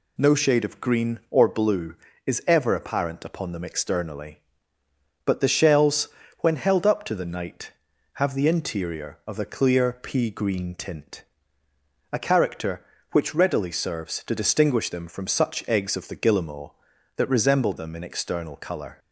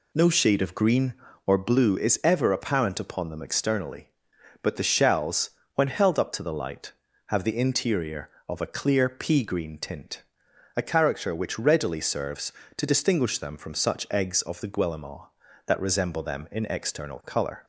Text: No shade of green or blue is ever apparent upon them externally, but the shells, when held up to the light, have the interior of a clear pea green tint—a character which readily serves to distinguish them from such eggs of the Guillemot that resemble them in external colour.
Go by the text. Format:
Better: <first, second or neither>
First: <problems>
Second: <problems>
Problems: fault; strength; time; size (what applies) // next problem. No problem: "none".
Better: second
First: says "night" for "light"; at 7.2 s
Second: none